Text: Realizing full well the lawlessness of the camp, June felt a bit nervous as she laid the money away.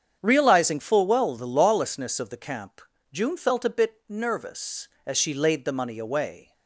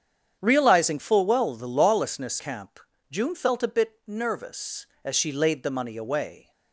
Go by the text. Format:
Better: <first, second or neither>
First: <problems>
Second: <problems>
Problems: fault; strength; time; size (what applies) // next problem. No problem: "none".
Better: first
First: starts louder than the rest; strong; until 1.2 s; 8 dB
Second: starts louder than the rest; strong; until 1.4 s; 8.5 dB // skips "of the"; at 2.3 s